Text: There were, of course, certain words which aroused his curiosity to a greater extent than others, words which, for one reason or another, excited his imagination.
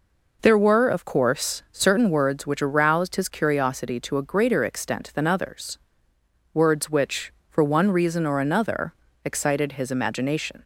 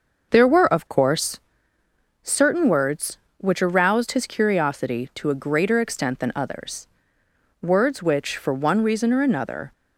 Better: first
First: none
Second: starts louder than the rest; noticeable; until 1.3 s; 6 dB // stops before "excited his imagination"; at 9.7 s

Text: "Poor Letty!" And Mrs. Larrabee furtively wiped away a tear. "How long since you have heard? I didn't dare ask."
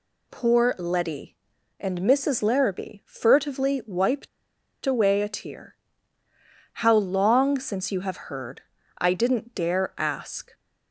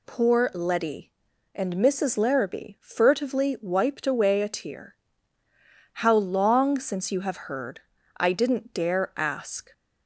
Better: second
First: pauses between "wiped" and "away"; noticeable; at 4.2 s; 0.57 s long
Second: none

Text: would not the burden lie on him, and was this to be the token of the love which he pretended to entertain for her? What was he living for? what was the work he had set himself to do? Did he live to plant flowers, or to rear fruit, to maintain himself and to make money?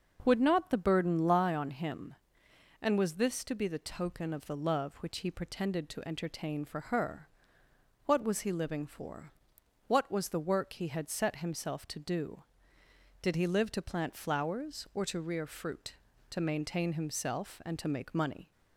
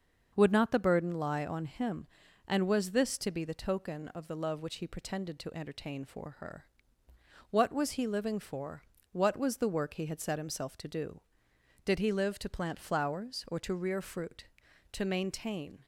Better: first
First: starts louder than the rest; noticeable; until 1.2 s; 6 dB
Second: starts louder than the rest; until 1.3 s; 6.5 dB // stops before "himself and to make money"; at 15.8 s

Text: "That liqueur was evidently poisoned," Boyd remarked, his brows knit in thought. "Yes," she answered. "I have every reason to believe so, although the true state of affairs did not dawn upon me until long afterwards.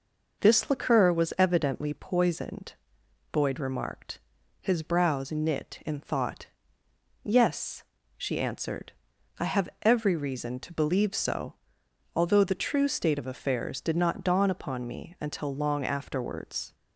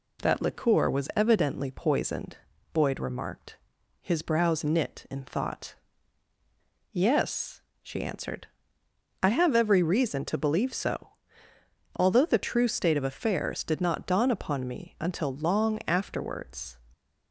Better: second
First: says "This" for "That"; at 0.3 s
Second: none

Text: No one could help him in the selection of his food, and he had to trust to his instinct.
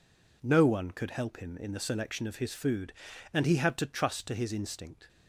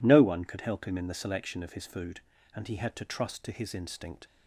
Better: neither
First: none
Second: none

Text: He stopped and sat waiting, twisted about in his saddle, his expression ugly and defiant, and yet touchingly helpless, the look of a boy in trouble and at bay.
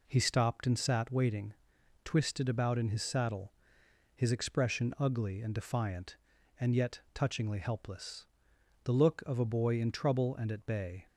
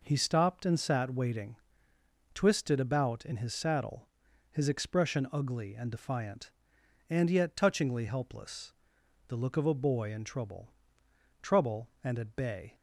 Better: first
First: none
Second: says "trouble" twice; at 11.4 s

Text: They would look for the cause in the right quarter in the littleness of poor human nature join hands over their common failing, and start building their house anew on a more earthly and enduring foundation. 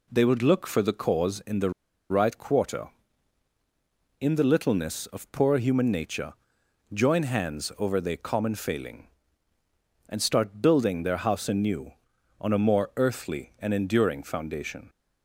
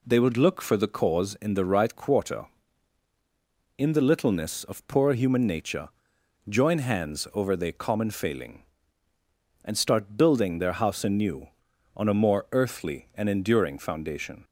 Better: second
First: pauses between "the" and "right"; at 1.6 s; 0.40 s long // pauses between "nature" and "join"; noticeable; at 6.3 s; 0.60 s long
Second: pauses between "nature" and "join"; noticeable; at 5.8 s; 0.60 s long

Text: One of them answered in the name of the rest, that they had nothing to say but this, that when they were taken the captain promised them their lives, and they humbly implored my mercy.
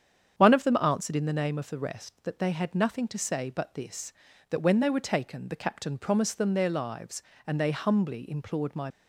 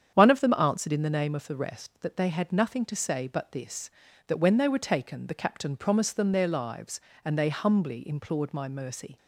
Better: second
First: starts louder than the rest; strong; until 1.3 s; 8 dB // stops before "mercy"; at 8.9 s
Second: starts louder than the rest; strong; until 1.1 s; 8.5 dB

